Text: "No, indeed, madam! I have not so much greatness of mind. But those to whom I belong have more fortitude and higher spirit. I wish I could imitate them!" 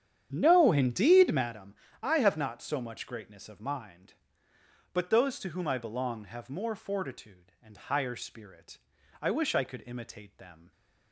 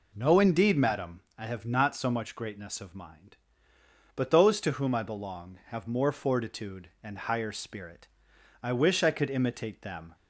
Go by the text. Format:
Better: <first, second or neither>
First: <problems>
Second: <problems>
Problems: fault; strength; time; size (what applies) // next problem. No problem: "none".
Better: second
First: starts louder than the rest; strong; until 1.6 s; 9 dB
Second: none